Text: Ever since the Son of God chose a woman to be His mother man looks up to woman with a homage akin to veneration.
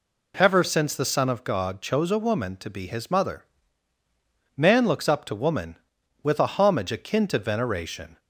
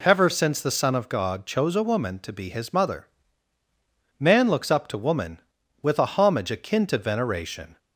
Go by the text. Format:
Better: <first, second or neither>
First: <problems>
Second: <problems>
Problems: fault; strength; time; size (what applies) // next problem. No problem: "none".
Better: neither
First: pauses between "mother" and "man"; at 3.4 s; 1.1 s long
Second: pauses between "mother" and "man"; at 3.0 s; 1.1 s long